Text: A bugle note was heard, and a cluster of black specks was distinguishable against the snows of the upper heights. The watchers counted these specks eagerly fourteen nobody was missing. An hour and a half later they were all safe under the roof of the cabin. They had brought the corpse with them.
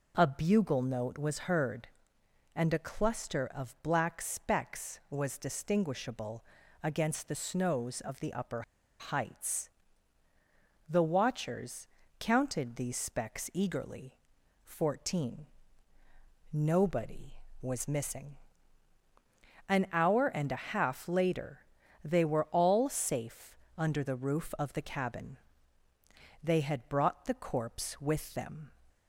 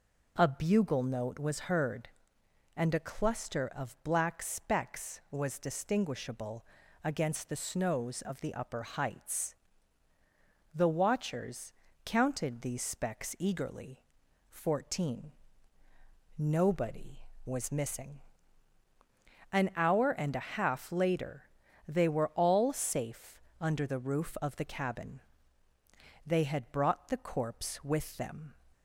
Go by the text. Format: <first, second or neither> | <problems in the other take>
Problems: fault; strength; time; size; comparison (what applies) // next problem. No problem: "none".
second | pauses between "distinguishable" and "against"; at 6.4 s; 0.40 s long; also in the second // pauses between "upper" and "heights"; at 8.6 s; 0.37 s long // pauses between "watchers" and "counted"; slight; at 11.8 s; 0.32 s long; slight in the second // pauses between "eagerly" and "fourteen"; noticeable; at 14.1 s; 0.50 s long; noticeable in the second // pauses between "fourteen" and "nobody"; at 15.4 s; 1.0 s long; also in the second // pauses between "later" and "they"; at 21.5 s; 0.44 s long; also in the second // pauses between "safe" and "under"; slight; at 23.5 s; 0.22 s long; slight in the second